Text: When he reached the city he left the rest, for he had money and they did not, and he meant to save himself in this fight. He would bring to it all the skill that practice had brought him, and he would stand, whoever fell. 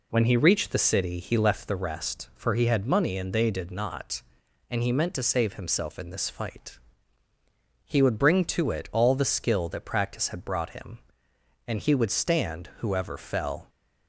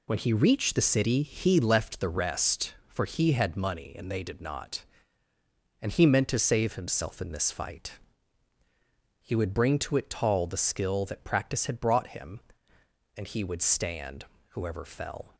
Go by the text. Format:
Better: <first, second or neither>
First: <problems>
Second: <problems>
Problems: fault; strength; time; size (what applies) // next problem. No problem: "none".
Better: first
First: none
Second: says "tall" for "all"; at 10.0 s